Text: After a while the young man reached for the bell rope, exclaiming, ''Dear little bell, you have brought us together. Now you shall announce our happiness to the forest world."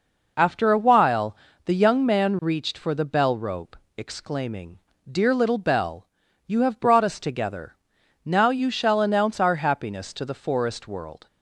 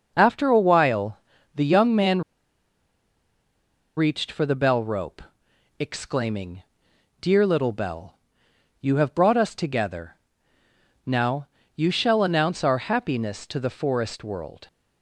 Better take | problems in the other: first | pauses between "while" and "the"; at 1.1 s; 0.38 s long; slight in the first // pauses between "man" and "reached"; strong; at 2.2 s; 1.7 s long // pauses between "Now" and "you"; slight; at 11.4 s; 0.30 s long

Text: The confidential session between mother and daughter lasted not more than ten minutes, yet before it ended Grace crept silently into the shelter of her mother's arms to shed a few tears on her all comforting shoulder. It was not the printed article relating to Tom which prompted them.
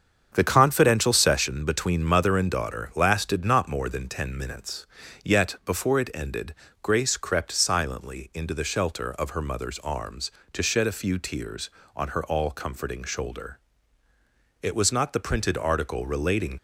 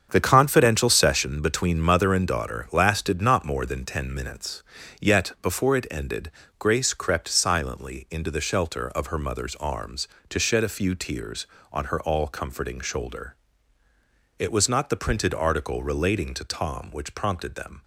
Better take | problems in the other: second | starts louder than the rest; strong; until 1.3 s; 7.5 dB; strong in the second // pauses between "ended" and "Grace"; slight; at 6.5 s; 0.26 s long; slight in the second // stops before "to Tom which prompted them"; at 16.5 s

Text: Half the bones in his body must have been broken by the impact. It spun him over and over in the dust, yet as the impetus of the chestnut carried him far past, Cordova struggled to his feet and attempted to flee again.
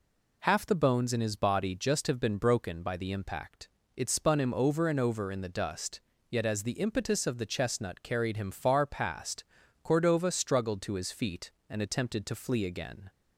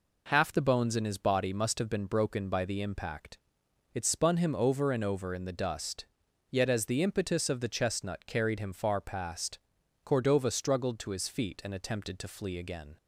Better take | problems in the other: second | says "just" for "must"; at 1.7 s

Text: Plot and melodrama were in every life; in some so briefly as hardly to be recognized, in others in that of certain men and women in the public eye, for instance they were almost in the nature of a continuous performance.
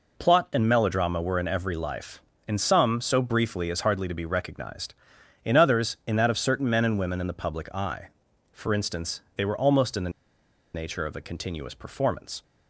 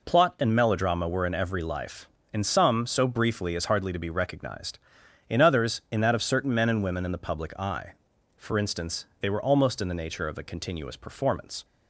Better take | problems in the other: second | pauses between "the" and "nature"; noticeable; at 10.1 s; 0.64 s long

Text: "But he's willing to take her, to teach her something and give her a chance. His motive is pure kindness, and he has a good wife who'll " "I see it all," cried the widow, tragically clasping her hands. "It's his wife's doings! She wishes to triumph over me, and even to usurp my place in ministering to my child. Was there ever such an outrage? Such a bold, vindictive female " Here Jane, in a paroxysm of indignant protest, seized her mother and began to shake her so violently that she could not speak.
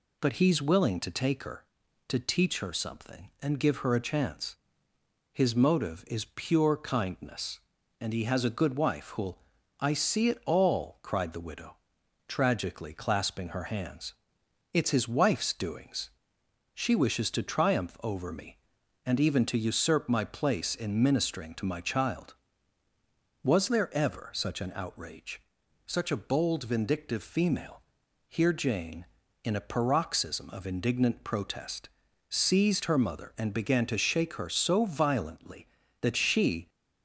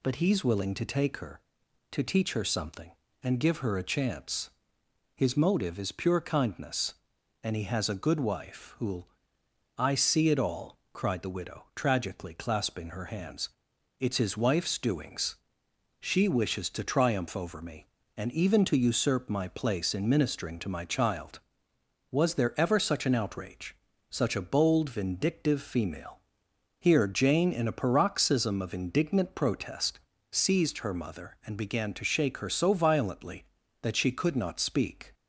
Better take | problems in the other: second | stops before "could not speak"; at 36.6 s

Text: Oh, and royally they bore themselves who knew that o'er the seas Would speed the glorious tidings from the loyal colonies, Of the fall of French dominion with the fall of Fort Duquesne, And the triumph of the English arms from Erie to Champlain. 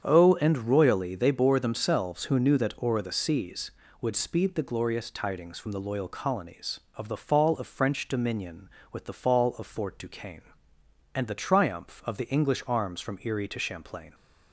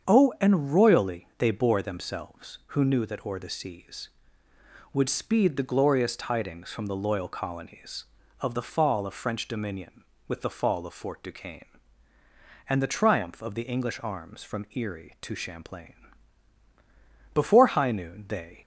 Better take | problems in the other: first | starts louder than the rest; strong; until 1.1 s; 7.5 dB; strong in the first // goes on to say "Before high noon they"; noticeable; from 17.3 s on; 1.2 s long

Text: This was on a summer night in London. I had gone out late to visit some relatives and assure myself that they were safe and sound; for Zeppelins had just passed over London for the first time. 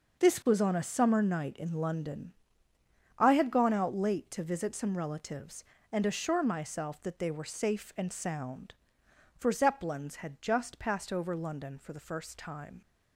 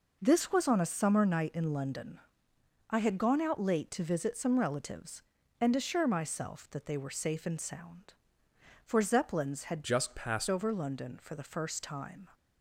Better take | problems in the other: first | changes voice from "just" to "passed"; from 9.8 to 10.4 s; 0.6 s long

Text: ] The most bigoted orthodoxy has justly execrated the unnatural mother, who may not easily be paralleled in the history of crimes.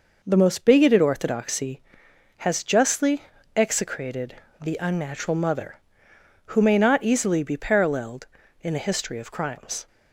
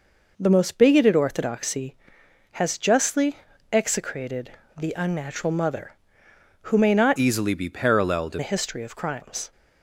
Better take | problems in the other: first | pauses between "justly" and "execrated"; slight; at 3.3 s; 0.34 s long; slight in the first // pauses between "execrated" and "the"; slight; at 4.5 s; 0.26 s long; slight in the first // changes voice from "easily" to "in"; from 7.1 to 8.3 s; 1.2 s long

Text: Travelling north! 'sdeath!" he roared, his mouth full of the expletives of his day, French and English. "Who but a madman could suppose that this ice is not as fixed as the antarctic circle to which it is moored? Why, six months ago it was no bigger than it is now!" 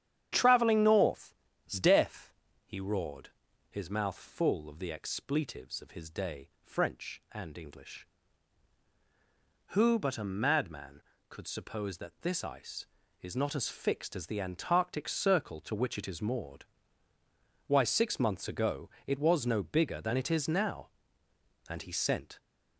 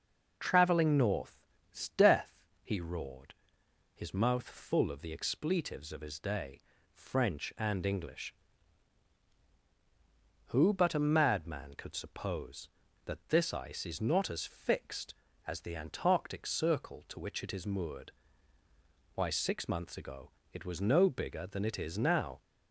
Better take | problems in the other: second | starts louder than the rest; strong; until 1.7 s; 9.5 dB // pauses between "ago" and "it"; slight; at 18.8 s; 0.16 s long; slight in the second // goes on to say "And he sent"; noticeable; from 21.6 s on; 0.70 s long

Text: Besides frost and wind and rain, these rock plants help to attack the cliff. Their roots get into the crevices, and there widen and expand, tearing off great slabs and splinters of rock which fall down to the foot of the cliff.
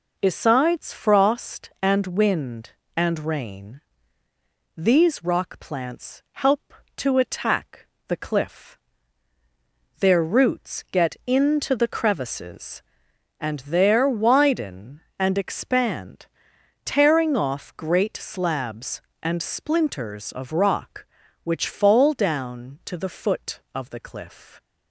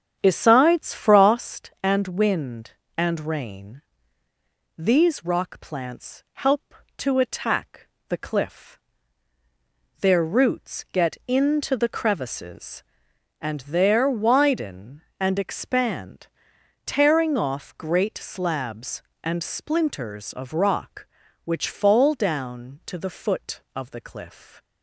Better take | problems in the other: first | starts louder than the rest; strong; until 1.6 s; 8 dB // pauses between "attack" and "the"; slight; at 7.8 s; 0.22 s long; slight in the first

